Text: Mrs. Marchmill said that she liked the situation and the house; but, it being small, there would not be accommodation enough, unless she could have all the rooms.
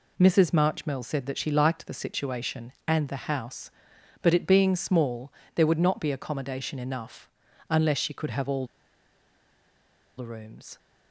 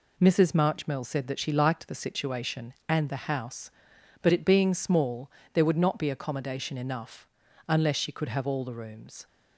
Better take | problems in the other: second | pauses between "all" and "the"; strong; at 8.6 s; 1.5 s long

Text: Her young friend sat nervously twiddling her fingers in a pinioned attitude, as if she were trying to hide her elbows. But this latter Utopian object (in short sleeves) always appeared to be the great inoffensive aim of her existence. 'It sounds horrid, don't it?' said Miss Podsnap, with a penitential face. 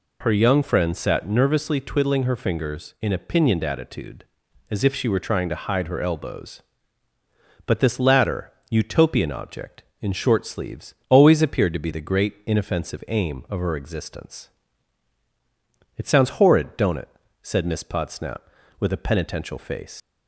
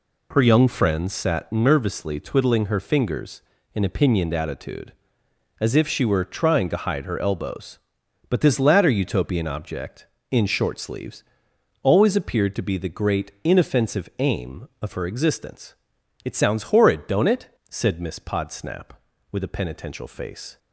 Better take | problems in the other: second | pauses between "latter" and "Utopian"; slight; at 8.5 s; 0.18 s long // leaves "face" unfinished; at 20.0 s; 115 ms

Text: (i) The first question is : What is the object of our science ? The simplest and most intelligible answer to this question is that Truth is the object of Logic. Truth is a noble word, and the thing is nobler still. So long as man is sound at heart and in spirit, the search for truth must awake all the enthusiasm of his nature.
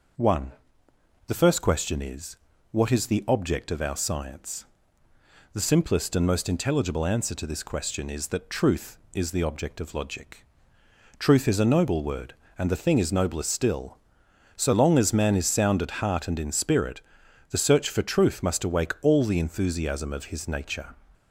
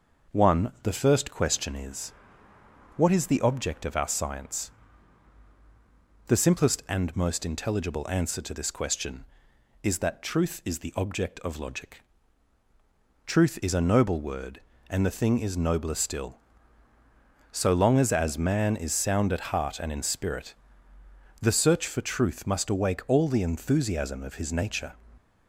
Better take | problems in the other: first | starts louder than the rest; noticeable; until 1.4 s; 6 dB // says "as" twice; at 18.1 s

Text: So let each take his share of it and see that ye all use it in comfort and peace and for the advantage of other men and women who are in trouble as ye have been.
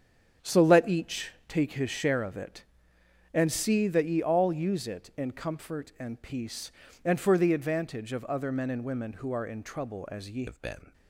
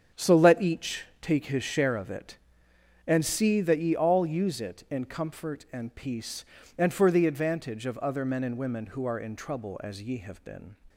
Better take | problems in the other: second | starts louder than the rest; strong; until 1.5 s; 7.5 dB; strong in the second // pauses between "each" and "take"; slight; at 1.3 s; 0.16 s long; slight in the second // changes voice at "have"; from 10.4 s on; 0.5 s long

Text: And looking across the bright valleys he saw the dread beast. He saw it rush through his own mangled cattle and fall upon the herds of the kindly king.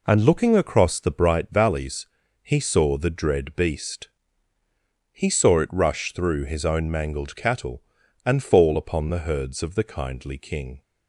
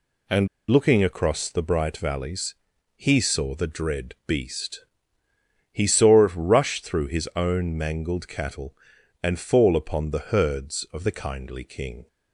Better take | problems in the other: first | pauses between "And" and "looking"; slight; at 0.4 s; 0.23 s long // pauses between "valleys" and "he"; at 2.5 s; 0.40 s long; slight in the first

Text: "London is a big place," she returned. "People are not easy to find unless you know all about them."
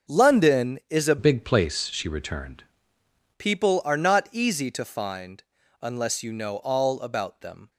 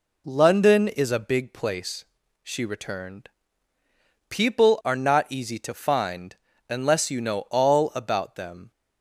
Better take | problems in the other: second | starts louder than the rest; until 1.2 s; 6.5 dB // changes voice from "big" to "returned"; from 1.1 to 2.6 s; 1.5 s long // pauses between "find" and "unless"; at 5.4 s; 0.40 s long; slight in the second

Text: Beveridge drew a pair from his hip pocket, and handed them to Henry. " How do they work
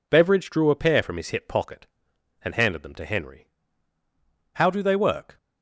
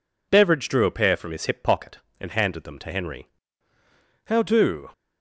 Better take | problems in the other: first | stops before "they work"; at 4.9 s

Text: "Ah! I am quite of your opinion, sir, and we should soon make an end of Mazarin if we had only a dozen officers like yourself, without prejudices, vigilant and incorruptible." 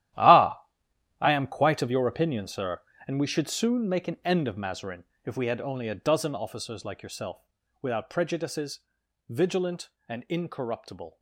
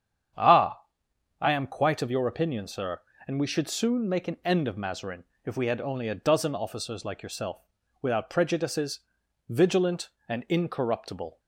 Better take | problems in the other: second | gets quieter; strong; throughout; 14 dB // starts louder than the rest; strong; until 1.7 s; 13 dB; strong in the second // pauses between "Mazarin" and "if"; slight; at 5.0 s; 0.20 s long; slight in the second

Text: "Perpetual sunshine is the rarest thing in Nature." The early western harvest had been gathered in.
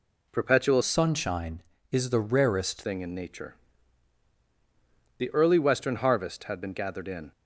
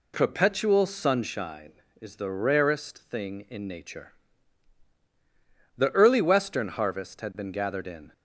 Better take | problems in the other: second | changes voice from "sunshine" to "rarest"; from 0.8 to 2.8 s; 2.0 s long

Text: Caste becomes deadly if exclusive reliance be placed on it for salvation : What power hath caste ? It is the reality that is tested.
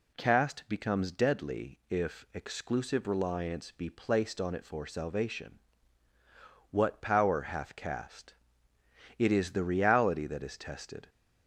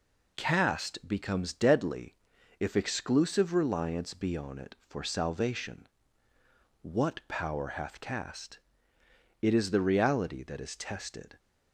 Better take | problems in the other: first | pauses between "deadly" and "if"; at 2.1 s; 0.42 s long // skips "placed"; at 4.3 s

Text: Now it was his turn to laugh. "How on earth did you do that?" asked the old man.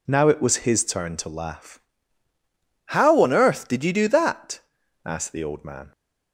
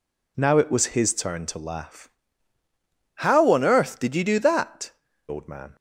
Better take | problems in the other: first | skips "asked the"; at 5.0 s

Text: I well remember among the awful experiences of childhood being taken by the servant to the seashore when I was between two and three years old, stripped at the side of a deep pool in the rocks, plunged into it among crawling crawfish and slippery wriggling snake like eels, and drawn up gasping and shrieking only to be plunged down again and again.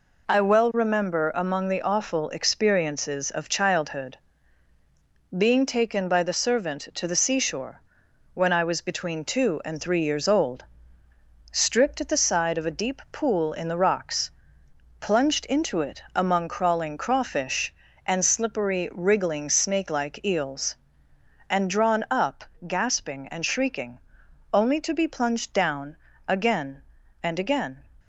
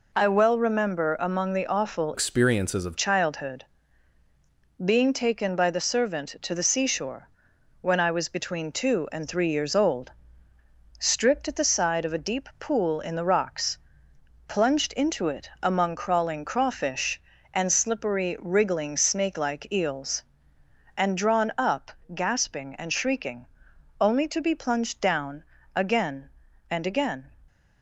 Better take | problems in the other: first | changes voice from "experiences" to "of"; from 2.1 to 2.9 s; 0.8 s long // pauses between "childhood" and "being"; at 3.6 s; 1.2 s long; also in the first // pauses between "seashore" and "when"; noticeable; at 7.2 s; 0.52 s long; noticeable in the first // pauses between "up" and "gasping"; slight; at 21.9 s; 0.24 s long; slight in the first // pauses between "shrieking" and "only"; noticeable; at 23.4 s; 0.54 s long; noticeable in the first // pauses between "down" and "again"; slight; at 25.4 s; 0.32 s long; slight in the first

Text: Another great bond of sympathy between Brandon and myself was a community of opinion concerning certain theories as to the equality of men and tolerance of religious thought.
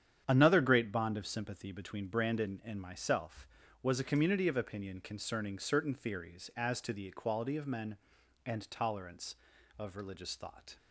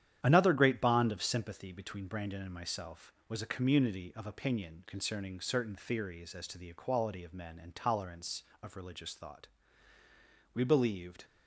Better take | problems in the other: first | starts louder than the rest; strong; until 1.2 s; 10 dB; strong in the first // goes on to say "We believed"; noticeable; from 10.5 s on; 0.72 s long

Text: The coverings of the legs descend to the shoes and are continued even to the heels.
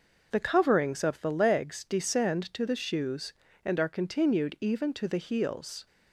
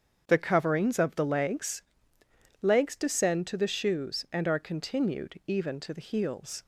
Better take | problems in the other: first | starts louder than the rest; strong; until 1.2 s; 7.5 dB // says "legs" twice; at 2.6 s

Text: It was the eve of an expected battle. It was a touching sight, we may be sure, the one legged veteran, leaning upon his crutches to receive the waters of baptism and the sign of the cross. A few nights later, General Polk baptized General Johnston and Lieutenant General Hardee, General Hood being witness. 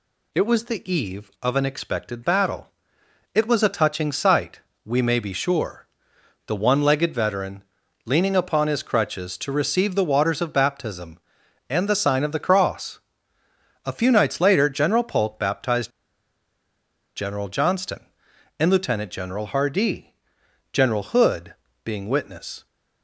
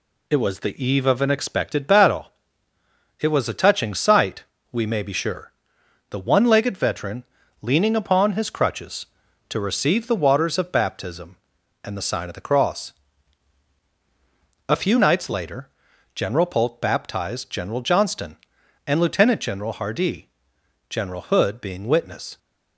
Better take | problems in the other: second | pauses between "baptized" and "General"; strong; at 15.9 s; 1.2 s long // pauses between "Hood" and "being"; slight; at 21.5 s; 0.30 s long

